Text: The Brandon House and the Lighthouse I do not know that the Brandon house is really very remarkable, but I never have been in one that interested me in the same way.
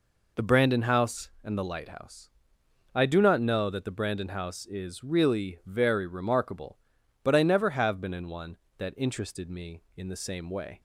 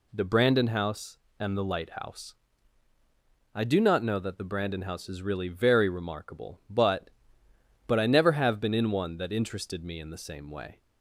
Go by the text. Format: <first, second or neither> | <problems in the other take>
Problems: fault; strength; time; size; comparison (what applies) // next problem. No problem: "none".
first | pauses between "Lighthouse" and "I"; at 2.3 s; 1.2 s long; noticeable in the first // says "but" twice; at 7.8 s